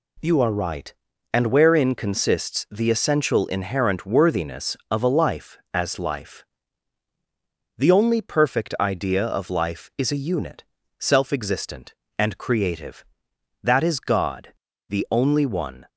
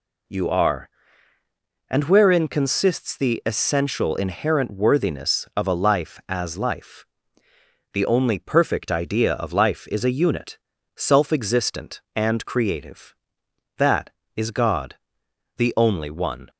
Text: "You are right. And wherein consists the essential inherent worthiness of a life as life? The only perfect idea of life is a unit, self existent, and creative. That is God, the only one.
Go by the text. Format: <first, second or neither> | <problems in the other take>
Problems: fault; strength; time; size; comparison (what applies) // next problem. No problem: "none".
first | skips "right"; at 1.3 s